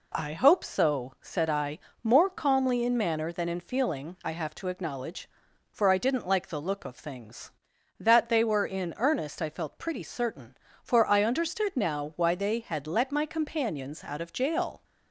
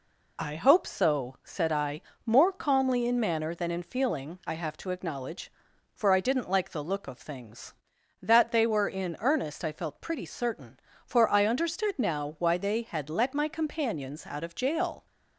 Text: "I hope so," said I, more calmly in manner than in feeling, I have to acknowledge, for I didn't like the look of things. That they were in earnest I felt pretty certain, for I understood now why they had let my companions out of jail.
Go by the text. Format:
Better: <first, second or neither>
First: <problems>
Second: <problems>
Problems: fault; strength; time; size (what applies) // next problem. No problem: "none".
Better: first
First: none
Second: loses the start of "I"; at 0.3 s; 45 ms